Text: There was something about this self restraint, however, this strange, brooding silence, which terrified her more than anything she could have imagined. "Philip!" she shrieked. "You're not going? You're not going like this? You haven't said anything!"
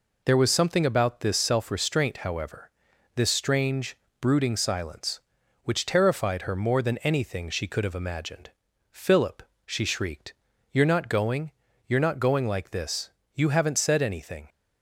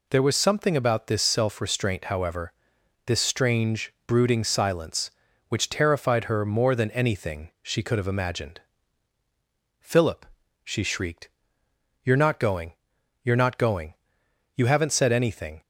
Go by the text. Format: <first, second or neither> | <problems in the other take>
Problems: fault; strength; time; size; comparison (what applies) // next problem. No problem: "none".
first | skips "like this"; at 14.2 s